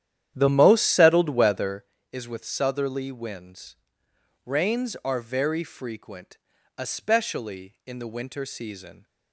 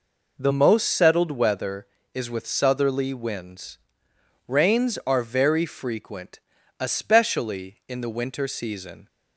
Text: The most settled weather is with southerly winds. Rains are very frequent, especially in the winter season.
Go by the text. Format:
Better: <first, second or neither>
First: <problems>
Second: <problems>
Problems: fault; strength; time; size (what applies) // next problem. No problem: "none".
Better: second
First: starts louder than the rest; strong; until 1.9 s; 10.5 dB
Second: none